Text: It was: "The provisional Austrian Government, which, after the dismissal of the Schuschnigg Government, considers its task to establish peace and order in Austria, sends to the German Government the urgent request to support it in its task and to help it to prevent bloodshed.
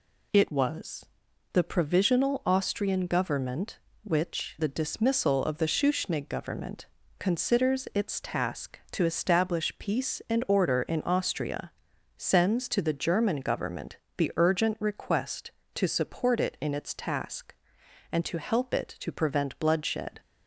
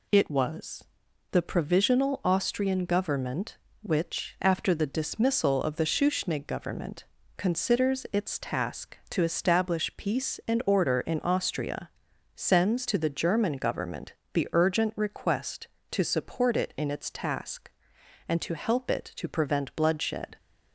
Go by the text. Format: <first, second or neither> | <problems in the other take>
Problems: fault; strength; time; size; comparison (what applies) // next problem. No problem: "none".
second | skips "after"; at 4.5 s // pauses between "Government" and "the"; slight; at 13.9 s; 0.20 s long; slight in the second